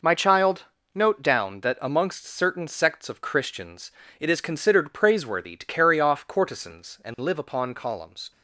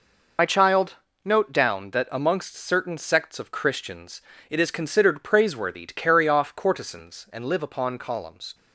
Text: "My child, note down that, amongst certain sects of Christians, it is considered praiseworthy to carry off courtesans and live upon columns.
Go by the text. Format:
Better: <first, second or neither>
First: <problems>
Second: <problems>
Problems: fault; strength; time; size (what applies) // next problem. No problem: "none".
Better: first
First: none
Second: loses the start of "My"; at 0.3 s; 55 ms